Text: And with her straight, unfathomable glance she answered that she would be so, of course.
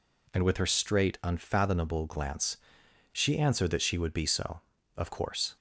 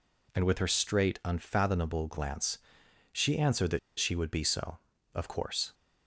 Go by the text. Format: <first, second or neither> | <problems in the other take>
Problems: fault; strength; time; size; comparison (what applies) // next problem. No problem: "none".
first | pauses between "glance" and "she"; noticeable; at 2.5 s; 0.54 s long; noticeable in the first // pauses between "that" and "she"; slight; at 3.7 s; 0.20 s long